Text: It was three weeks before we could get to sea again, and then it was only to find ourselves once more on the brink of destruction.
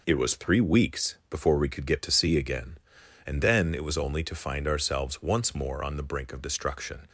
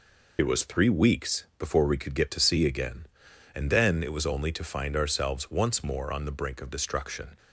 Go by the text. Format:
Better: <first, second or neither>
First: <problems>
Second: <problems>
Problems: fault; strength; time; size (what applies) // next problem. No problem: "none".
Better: first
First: none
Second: loses the start of "It"; at 0.3 s; 40 ms